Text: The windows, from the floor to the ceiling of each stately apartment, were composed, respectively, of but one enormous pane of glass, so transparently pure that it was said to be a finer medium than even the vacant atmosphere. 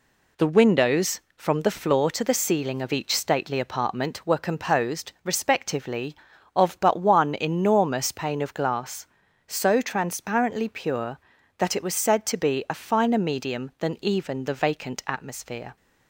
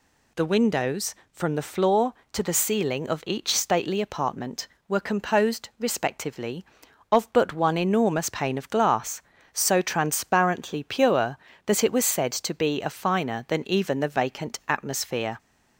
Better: first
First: none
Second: skips "medium"; at 13.4 s

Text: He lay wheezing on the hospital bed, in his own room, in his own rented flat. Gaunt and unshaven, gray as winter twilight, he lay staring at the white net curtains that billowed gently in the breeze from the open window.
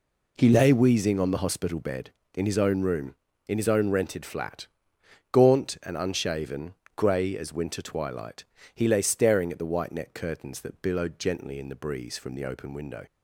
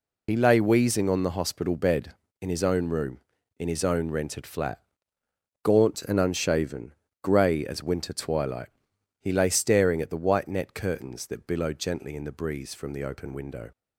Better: first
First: none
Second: loses the start of "He"; at 0.2 s; 50 ms

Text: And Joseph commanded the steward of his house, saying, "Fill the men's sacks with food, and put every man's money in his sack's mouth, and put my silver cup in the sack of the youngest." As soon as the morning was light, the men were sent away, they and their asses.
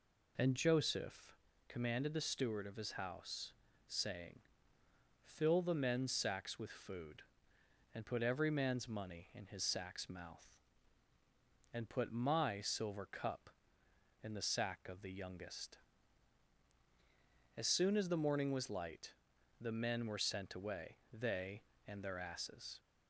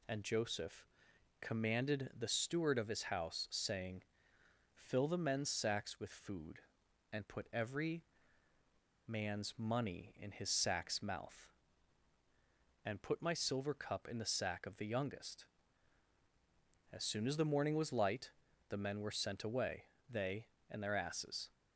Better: first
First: pauses between "Joseph" and "commanded"; slight; at 1.3 s; 0.32 s long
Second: pauses between "Joseph" and "commanded"; noticeable; at 0.8 s; 0.56 s long // pauses between "every" and "man's"; at 8.0 s; 1.0 s long

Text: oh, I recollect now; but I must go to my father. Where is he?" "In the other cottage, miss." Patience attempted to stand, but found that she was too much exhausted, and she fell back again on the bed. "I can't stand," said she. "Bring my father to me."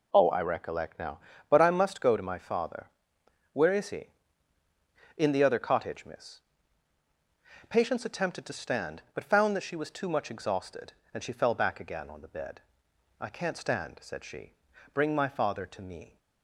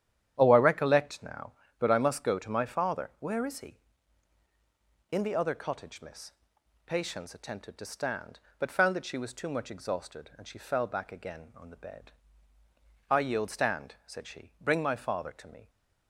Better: first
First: none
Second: starts louder than the rest; strong; until 1.3 s; 10 dB // says "yield" for "can't"; at 13.1 s

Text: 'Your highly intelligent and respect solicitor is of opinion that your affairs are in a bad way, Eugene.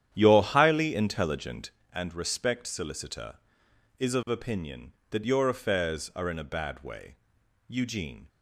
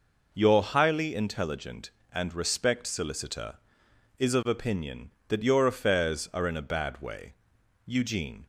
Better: second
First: starts louder than the rest; strong; until 1.8 s; 10 dB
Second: none

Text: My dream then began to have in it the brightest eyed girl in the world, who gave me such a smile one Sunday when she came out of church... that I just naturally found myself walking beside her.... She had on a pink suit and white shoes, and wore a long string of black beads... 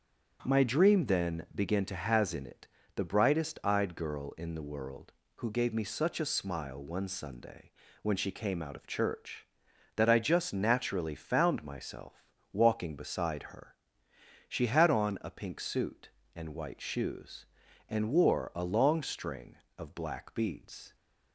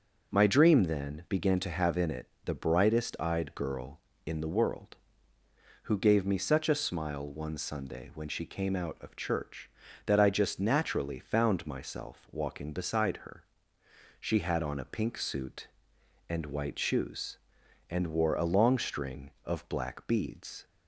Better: second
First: starts louder than the rest; strong; until 1.4 s; 7.5 dB // says "has" for "have"; at 1.9 s // pauses between "it" and "the"; slight; at 2.6 s; 0.28 s long // pauses between "Sunday" and "when"; slight; at 7.7 s; 0.30 s long // pauses between "myself" and "walking"; slight; at 12.2 s; 0.28 s long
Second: starts louder than the rest; until 1.3 s; 6 dB // pauses between "it" and "the"; slight; at 2.2 s; 0.16 s long

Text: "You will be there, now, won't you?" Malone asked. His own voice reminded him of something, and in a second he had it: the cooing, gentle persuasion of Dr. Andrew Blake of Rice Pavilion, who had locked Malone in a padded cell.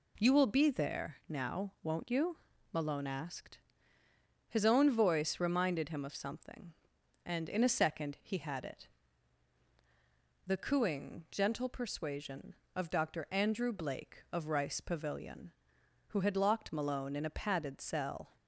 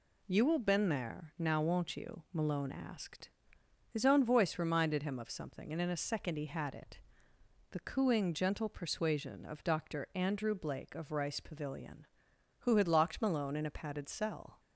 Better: first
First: none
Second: says "been" for "be"; at 0.5 s

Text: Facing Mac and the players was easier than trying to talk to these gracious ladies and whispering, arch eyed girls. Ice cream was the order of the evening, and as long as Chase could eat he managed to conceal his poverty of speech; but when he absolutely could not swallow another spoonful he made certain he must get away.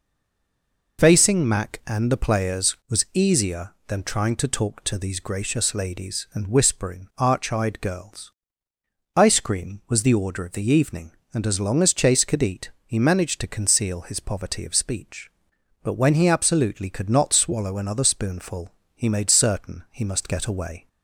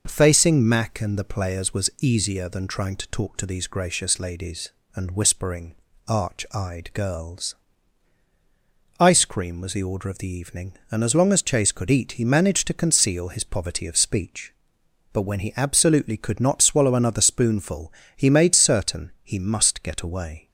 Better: second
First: stays silent before the first word; slight; until 0.9 s; 0.9 s long // pauses between "spoonful" and "he"; slight; at 18.7 s; 0.22 s long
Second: pauses between "spoonful" and "he"; slight; at 17.9 s; 0.24 s long

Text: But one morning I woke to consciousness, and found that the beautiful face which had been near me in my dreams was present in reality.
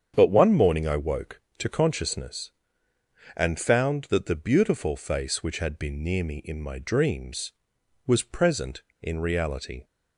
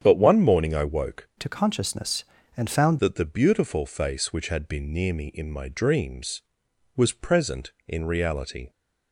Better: first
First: starts louder than the rest; strong; until 1.1 s; 8 dB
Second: starts louder than the rest; strong; until 1.0 s; 8 dB // changes voice from "to" to "found"; from 1.3 to 2.9 s; 1.6 s long

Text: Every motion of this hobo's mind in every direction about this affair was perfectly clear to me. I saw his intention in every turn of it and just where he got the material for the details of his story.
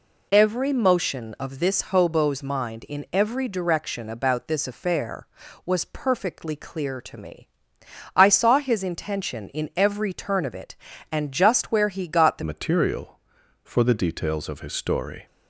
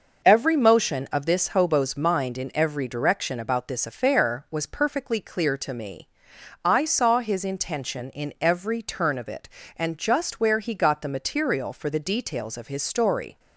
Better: second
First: changes voice at "material"; from 12.4 s on; 2.8 s long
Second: none

